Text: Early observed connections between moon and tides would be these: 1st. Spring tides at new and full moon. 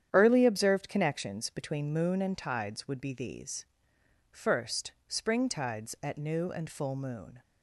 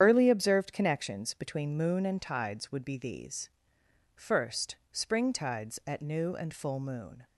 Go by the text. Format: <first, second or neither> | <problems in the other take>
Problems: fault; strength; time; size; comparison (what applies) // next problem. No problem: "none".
first | loses the start of "Early"; at 0.0 s; 45 ms // starts louder than the rest; strong; until 1.0 s; 9 dB; strong in the first